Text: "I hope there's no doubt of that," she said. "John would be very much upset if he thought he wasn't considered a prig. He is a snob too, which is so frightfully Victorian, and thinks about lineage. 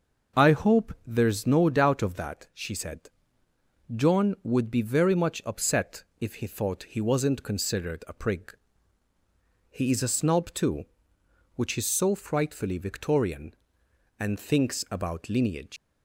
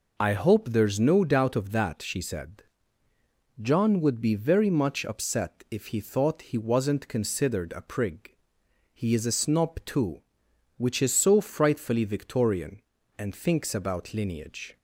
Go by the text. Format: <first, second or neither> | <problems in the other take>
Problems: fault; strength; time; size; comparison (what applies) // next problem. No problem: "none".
second | starts louder than the rest; until 1.4 s; 6 dB // pauses between "upset" and "if"; slight; at 6.0 s; 0.16 s long // leaves "lineage" unfinished; at 15.7 s; 140 ms